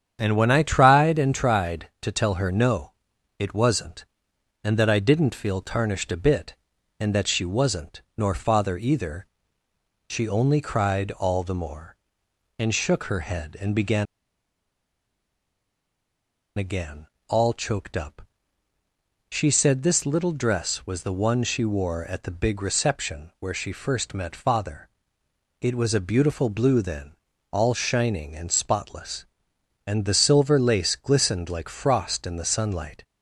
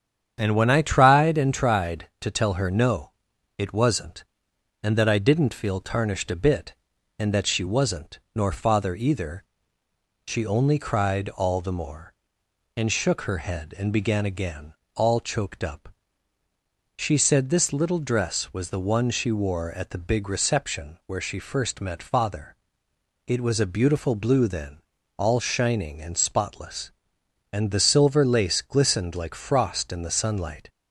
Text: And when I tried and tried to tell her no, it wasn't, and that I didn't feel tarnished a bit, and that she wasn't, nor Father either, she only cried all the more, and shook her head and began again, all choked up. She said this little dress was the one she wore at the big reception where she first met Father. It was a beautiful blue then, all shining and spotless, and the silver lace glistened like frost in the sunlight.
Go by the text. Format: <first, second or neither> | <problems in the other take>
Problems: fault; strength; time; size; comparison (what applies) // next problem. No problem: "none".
second | starts louder than the rest; strong; until 1.2 s; 8.5 dB; strong in the second // pauses between "began" and "again"; strong; at 14.0 s; 2.5 s long